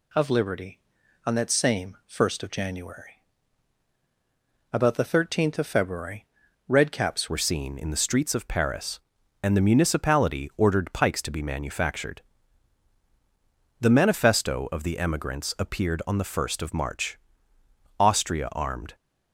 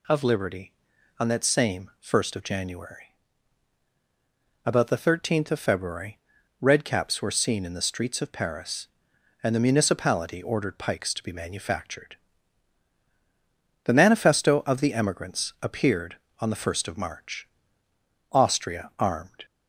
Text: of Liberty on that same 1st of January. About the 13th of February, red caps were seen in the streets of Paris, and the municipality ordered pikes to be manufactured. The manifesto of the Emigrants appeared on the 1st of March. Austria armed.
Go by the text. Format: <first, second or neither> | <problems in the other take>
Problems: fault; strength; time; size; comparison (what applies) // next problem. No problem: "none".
second | changes voice at "were"; from 7.2 s on; 11.7 s long